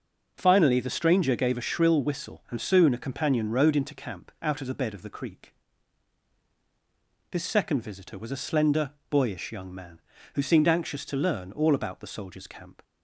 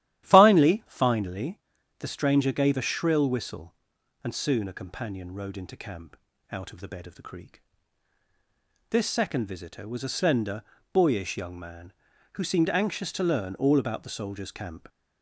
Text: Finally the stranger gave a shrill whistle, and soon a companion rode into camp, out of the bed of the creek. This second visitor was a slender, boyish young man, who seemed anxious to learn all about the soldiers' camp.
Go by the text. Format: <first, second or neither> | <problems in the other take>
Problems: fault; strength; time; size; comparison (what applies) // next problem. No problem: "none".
first | starts louder than the rest; strong; until 1.2 s; 12.5 dB // says "Finally" twice; at 0.8 s